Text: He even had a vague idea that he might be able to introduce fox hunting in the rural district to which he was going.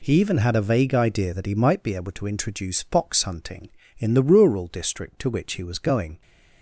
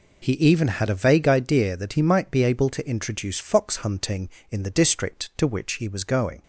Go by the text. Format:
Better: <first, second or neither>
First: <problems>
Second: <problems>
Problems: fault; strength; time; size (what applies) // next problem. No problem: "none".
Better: first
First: none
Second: skips "rural"; at 4.7 s